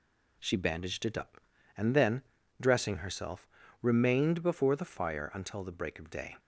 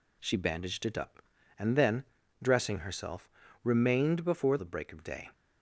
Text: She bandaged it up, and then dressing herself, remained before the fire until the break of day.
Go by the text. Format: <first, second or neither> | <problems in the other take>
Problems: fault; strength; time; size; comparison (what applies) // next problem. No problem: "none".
first | pauses between "then" and "dressing"; at 2.0 s; 0.38 s long; also in the first // skips "the fire until"; at 4.5 s